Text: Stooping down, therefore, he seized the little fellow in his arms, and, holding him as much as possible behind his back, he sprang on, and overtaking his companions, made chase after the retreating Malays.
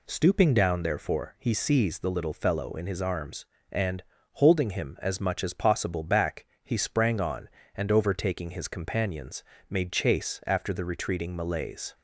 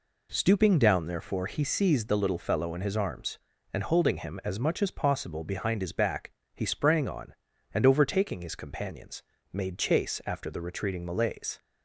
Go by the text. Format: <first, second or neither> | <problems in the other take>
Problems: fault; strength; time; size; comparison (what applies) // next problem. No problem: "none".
second | skips "behind his"; at 6.0 s